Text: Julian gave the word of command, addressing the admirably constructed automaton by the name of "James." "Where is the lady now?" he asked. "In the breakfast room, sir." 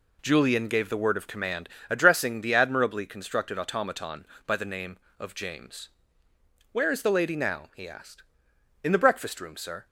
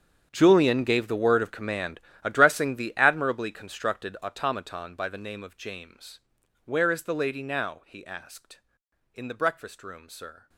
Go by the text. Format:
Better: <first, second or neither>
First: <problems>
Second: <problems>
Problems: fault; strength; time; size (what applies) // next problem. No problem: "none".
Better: first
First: none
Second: gets quieter; strong; throughout; 17.5 dB